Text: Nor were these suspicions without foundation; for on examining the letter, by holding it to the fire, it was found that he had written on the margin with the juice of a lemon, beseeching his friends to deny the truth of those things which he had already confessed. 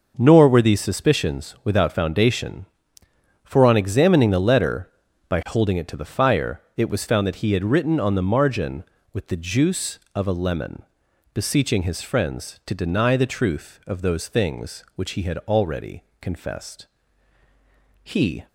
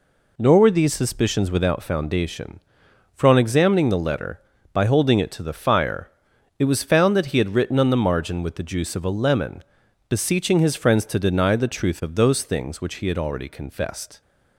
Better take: second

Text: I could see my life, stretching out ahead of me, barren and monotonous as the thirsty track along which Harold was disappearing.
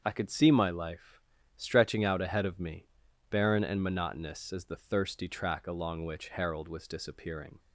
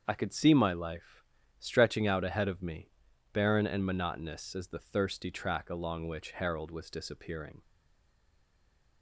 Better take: first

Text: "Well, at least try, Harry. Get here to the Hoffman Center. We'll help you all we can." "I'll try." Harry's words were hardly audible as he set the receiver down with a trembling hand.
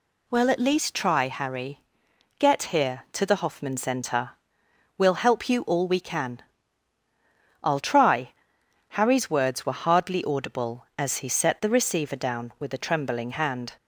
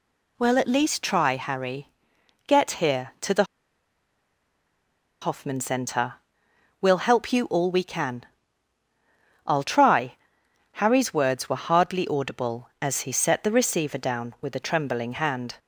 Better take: first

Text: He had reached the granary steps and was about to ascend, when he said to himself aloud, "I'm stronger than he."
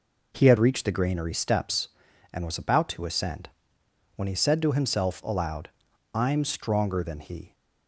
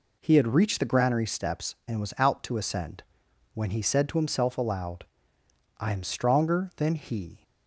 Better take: first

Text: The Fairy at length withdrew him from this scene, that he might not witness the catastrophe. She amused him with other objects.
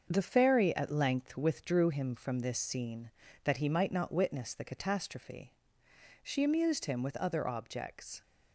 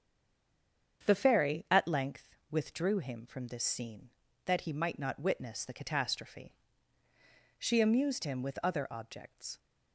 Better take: first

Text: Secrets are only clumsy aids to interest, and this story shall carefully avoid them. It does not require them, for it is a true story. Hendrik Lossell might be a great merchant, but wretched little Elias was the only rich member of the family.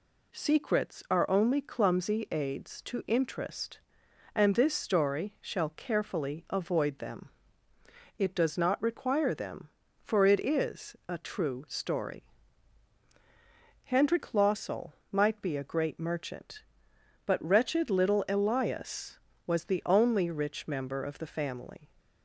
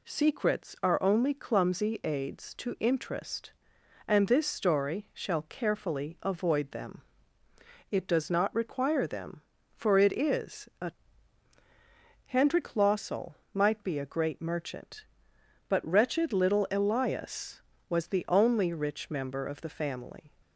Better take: first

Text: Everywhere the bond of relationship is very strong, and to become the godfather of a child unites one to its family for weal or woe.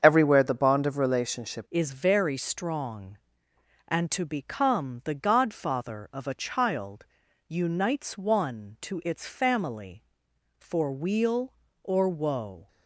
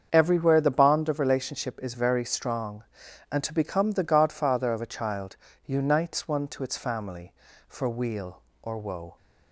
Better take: second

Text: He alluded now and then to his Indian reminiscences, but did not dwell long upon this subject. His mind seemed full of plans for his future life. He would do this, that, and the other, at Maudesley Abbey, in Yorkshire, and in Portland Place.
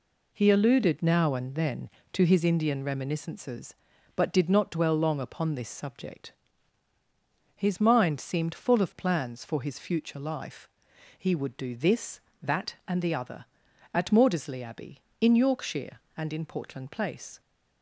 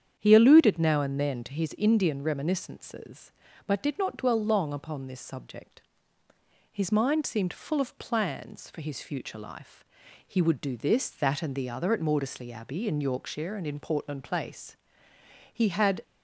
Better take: first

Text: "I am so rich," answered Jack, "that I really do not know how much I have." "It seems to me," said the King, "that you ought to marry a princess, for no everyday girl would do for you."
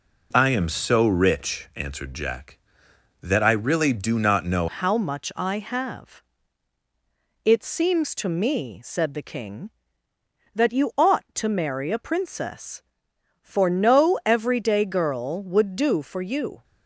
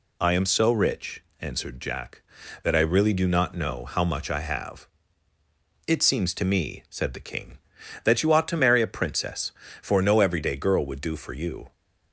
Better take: second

